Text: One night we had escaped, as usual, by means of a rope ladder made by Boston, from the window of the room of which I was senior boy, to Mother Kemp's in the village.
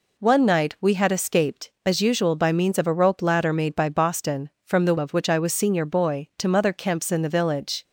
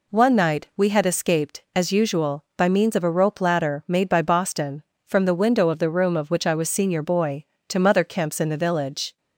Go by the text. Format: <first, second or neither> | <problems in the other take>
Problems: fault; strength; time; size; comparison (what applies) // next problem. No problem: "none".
second | skips "window of the room"; at 4.9 s